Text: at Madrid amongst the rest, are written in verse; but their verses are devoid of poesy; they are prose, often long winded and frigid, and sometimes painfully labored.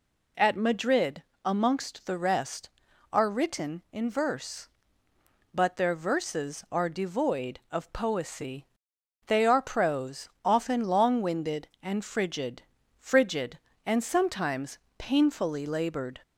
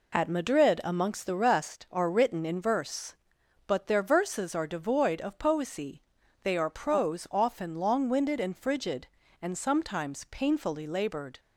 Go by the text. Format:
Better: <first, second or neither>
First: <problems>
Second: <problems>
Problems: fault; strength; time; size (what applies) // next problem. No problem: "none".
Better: second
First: pauses between "Madrid" and "amongst"; slight; at 1.2 s; 0.20 s long // says "frigid" twice; at 12.9 s // pauses between "sometimes" and "painfully"; slight; at 14.7 s; 0.22 s long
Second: none